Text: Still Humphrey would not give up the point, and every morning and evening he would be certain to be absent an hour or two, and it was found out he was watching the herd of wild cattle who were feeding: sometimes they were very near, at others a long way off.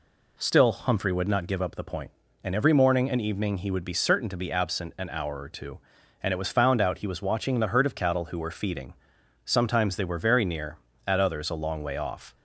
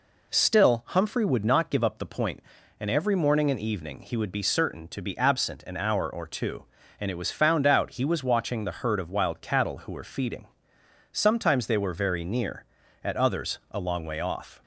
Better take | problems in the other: second | skips "wild"; at 7.9 s

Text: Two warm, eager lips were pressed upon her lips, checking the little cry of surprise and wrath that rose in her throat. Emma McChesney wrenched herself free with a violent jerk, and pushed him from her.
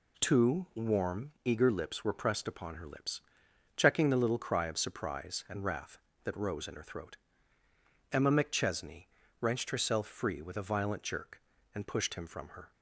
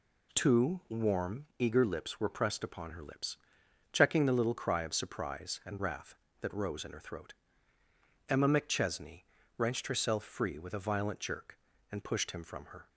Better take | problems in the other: neither | pauses between "McChesney" and "wrenched"; slight; the same in both

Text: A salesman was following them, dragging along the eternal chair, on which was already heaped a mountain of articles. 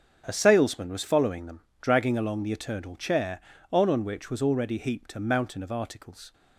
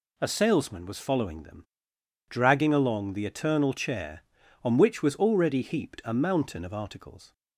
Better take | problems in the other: second | starts louder than the rest; strong; until 1.2 s; 7.5 dB // says "on" twice; at 3.9 s

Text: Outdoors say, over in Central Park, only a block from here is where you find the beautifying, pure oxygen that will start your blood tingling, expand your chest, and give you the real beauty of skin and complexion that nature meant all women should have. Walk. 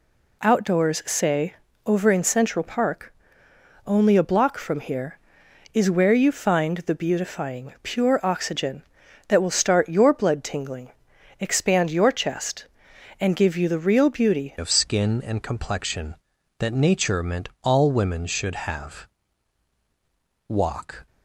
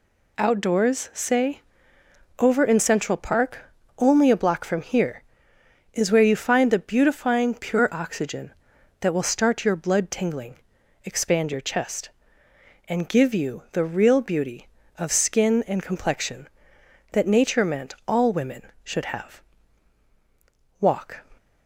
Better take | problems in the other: second | changes voice at "of"; from 14.5 s on; 6.5 s long

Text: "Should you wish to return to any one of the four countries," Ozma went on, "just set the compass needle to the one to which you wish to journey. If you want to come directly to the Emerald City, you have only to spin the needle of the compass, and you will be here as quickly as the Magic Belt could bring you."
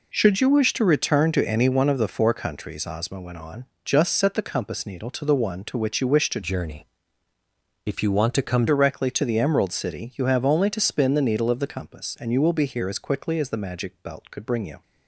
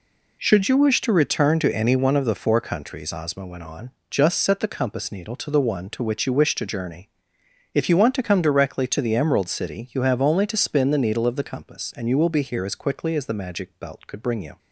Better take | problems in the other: second | changes voice from "journey" to "come"; from 6.4 to 8.6 s; 2.2 s long

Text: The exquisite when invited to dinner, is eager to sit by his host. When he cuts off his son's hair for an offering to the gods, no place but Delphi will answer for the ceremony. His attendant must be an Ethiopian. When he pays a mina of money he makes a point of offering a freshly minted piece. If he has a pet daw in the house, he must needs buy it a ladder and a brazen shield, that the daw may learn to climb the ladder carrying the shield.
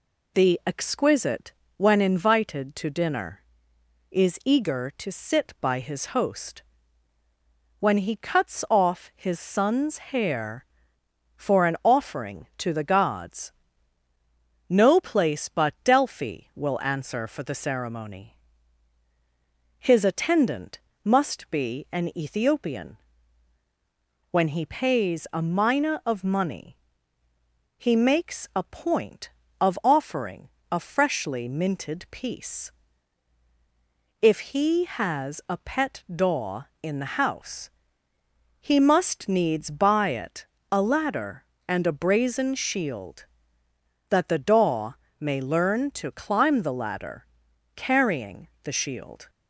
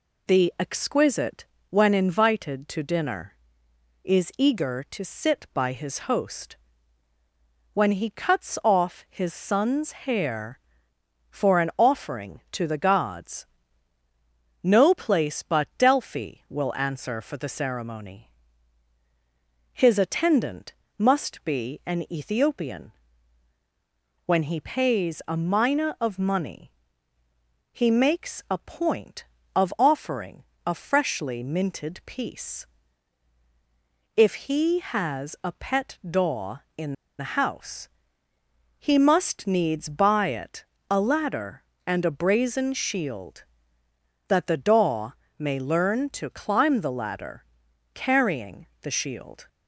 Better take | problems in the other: first | pauses between "exquisite" and "when"; slight; at 1.4 s; 0.24 s long; slight in the first // pauses between "attendant" and "must"; slight; at 20.7 s; 0.26 s long; slight in the first // pauses between "money" and "he"; at 26.7 s; 1.0 s long; also in the first // pauses between "offering" and "a"; slight; at 30.4 s; 0.24 s long; slight in the first // pauses between "in" and "the"; slight; at 36.9 s; 0.26 s long // pauses between "it" and "a"; slight; at 40.6 s; 0.26 s long; slight in the first // pauses between "daw" and "may"; slight; at 45.1 s; 0.26 s long; slight in the first // pauses between "ladder" and "carrying"; noticeable; at 47.4 s; 0.50 s long; noticeable in the first // pauses between "carrying" and "the"; slight; at 48.6 s; 0.16 s long; slight in the first

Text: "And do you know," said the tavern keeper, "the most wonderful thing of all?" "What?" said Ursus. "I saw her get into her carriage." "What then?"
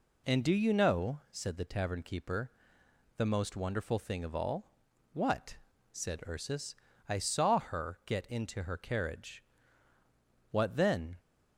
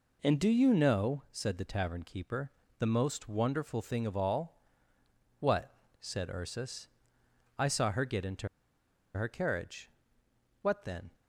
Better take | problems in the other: first | pauses between "into" and "her"; noticeable; at 8.4 s; 0.68 s long

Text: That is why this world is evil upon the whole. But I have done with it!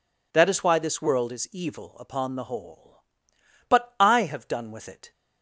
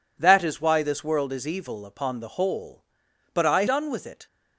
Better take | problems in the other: first | skips "have"; at 3.6 s

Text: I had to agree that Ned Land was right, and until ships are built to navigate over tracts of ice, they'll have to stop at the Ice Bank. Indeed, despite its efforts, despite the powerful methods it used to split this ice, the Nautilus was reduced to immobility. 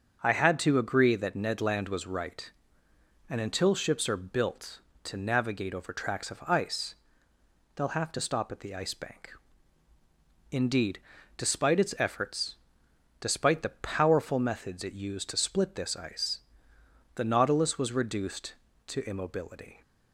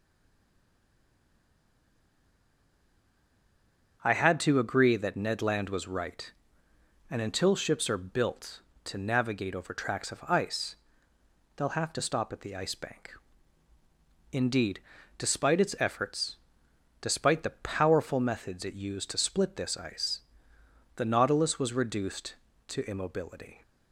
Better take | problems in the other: first | stays silent before the first word; strong; until 4.0 s; 4.0 s long // starts louder than the rest; until 5.0 s; 6.5 dB; strong in the first

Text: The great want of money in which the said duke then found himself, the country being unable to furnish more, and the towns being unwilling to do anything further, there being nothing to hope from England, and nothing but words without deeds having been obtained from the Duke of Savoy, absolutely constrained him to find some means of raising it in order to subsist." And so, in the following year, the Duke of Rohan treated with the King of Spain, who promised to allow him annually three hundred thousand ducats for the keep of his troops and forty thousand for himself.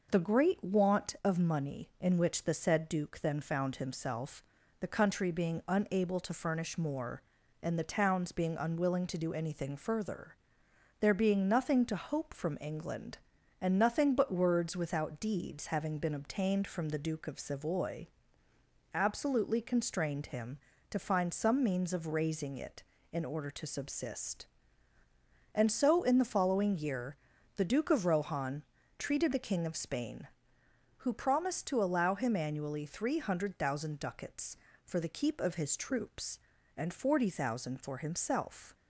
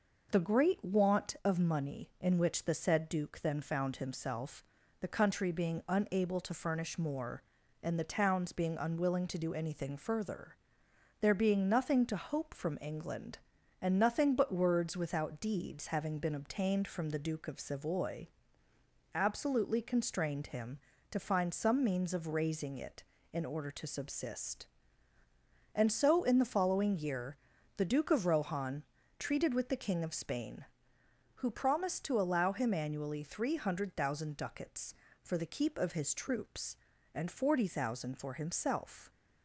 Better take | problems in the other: second | pauses between "Rohan" and "treated"; at 28.6 s; 0.38 s long; also in the second // skips "with"; at 29.3 s

